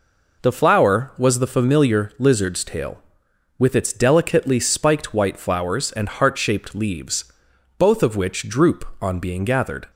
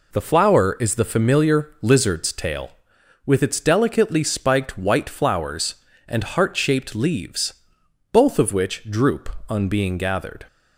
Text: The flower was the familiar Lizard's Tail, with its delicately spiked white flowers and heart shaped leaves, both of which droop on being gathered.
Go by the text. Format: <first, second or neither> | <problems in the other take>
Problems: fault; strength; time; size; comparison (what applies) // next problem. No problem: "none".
first | says "is" for "was"; at 0.7 s